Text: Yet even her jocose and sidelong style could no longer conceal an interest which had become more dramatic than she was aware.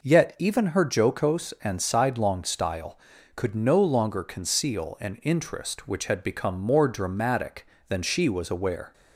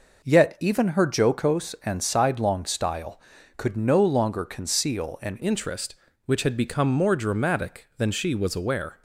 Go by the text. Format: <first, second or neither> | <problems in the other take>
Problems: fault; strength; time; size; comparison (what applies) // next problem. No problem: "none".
first | changes voice at "interest"; from 5.4 s on; 3.6 s long